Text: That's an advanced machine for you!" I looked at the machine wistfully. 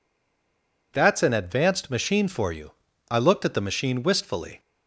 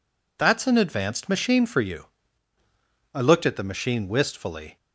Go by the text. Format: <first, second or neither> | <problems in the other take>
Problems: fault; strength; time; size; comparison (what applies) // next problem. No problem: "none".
second | stays silent before the first word; slight; until 0.9 s; 0.9 s long